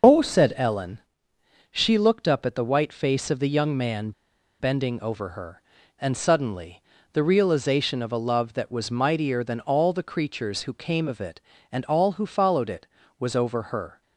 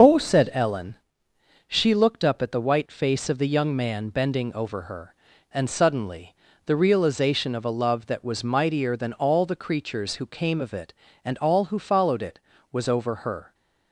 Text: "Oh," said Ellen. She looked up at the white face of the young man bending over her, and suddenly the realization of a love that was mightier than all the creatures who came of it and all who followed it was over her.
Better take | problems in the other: second | pauses between "man" and "bending"; noticeable; at 4.1 s; 0.49 s long // pauses between "suddenly" and "the"; slight; at 6.8 s; 0.30 s long; slight in the second

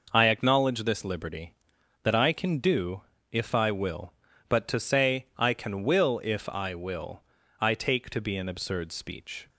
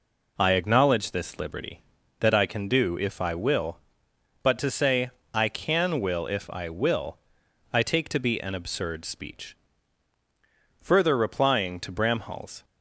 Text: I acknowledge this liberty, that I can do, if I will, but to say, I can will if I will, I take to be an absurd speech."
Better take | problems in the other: first | goes on to say "Further replying to Bramhall's"; strong; from 10.7 s on; 1.8 s long

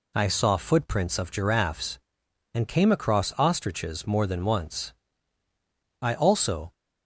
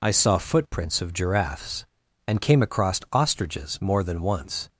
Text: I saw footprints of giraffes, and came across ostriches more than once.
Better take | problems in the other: second | goes on to say "I also"; noticeable; from 6.0 s on; 0.70 s long

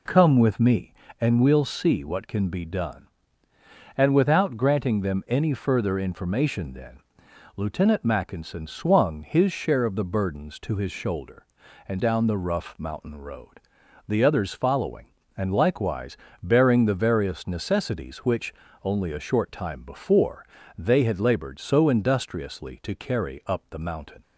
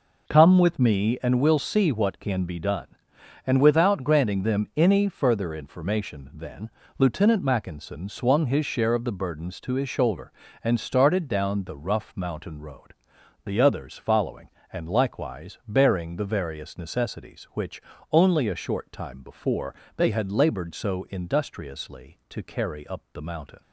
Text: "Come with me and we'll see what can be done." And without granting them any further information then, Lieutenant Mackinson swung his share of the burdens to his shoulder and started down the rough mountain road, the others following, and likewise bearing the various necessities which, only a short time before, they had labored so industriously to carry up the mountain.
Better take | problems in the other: second | skips "started"; at 12.0 s // pauses between "likewise" and "bearing"; slight; at 16.1 s; 0.28 s long

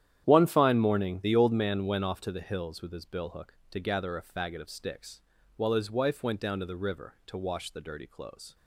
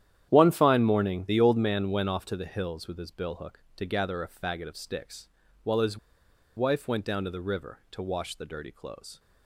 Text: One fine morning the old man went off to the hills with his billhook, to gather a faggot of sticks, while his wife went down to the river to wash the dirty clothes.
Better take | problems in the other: first | starts louder than the rest; strong; until 1.3 s; 10.5 dB; strong in the first // pauses between "his" and "wife"; noticeable; at 5.9 s; 0.59 s long

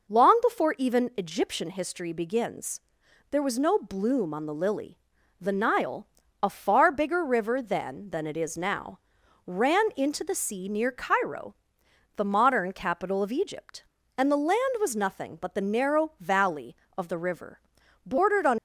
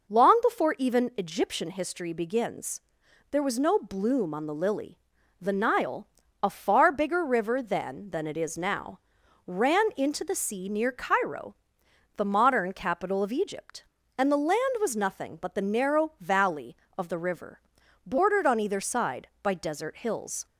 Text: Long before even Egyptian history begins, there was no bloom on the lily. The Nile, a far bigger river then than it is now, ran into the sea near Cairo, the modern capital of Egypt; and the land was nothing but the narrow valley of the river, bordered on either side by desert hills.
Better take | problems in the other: second | stops before "either side by desert hills"; at 18.5 s

